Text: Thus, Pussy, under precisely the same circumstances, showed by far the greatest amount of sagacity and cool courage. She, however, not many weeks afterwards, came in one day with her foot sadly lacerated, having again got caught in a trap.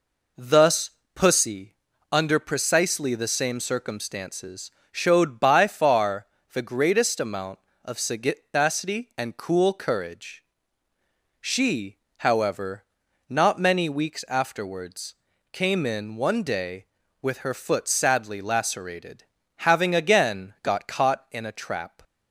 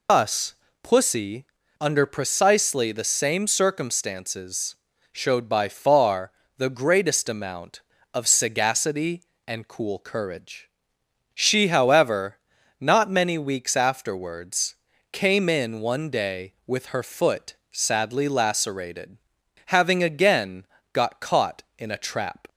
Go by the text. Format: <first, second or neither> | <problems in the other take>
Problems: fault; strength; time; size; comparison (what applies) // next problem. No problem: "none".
first | loses the start of "Thus"; at 0.0 s; 120 ms // pauses between "far" and "the"; slight; at 6.3 s; 0.26 s long; slight in the first // pauses between "foot" and "sadly"; slight; at 17.5 s; 0.16 s long // pauses between "again" and "got"; slight; at 20.6 s; 0.26 s long